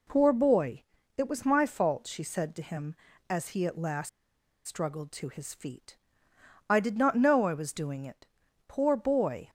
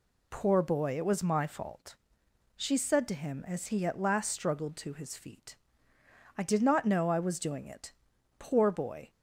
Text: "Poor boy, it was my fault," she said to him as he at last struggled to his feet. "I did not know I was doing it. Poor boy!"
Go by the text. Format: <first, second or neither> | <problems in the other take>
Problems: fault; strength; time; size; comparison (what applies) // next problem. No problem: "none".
second | pauses between "last" and "struggled"; noticeable; at 4.0 s; 0.56 s long